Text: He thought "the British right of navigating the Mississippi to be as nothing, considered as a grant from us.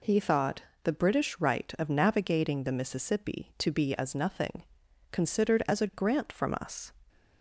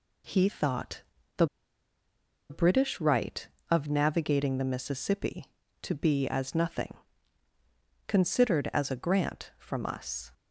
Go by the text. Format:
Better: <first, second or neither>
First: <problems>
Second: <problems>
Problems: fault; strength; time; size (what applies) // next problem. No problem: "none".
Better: first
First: pauses between "thought" and "the"; slight; at 0.6 s; 0.20 s long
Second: pauses between "thought" and "the"; slight; at 1.0 s; 0.34 s long // pauses between "the" and "British"; at 1.4 s; 1.0 s long